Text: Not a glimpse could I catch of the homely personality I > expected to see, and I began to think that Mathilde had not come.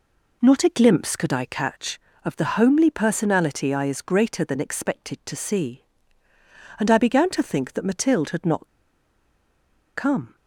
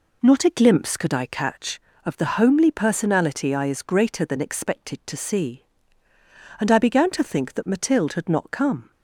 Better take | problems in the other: second | pauses between "not" and "come"; strong; at 8.6 s; 1.2 s long

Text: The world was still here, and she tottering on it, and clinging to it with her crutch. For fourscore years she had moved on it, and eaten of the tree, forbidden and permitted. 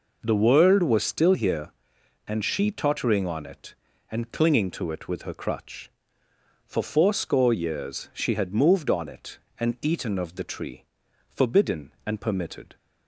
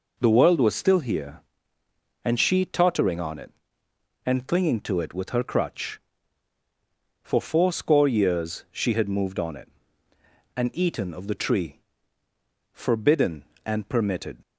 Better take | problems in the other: neither | none

